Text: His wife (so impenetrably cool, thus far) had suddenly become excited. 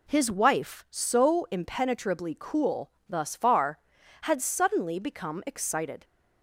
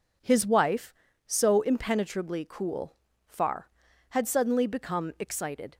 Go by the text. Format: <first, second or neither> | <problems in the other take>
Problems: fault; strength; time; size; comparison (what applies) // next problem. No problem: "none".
first | skips "thus"; at 3.1 s